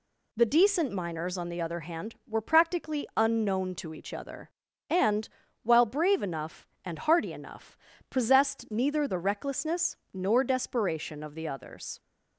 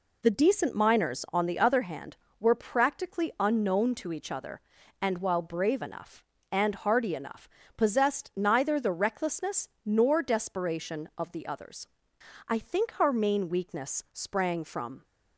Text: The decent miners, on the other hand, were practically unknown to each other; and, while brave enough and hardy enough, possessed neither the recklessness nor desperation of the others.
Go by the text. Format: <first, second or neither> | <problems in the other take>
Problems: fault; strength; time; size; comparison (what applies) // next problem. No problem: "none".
first | pauses between "recklessness" and "nor"; slight; at 9.6 s; 0.18 s long; slight in the first // goes on to say "I think our main weakness sprang from"; strong; from 12.4 s on; 2.5 s long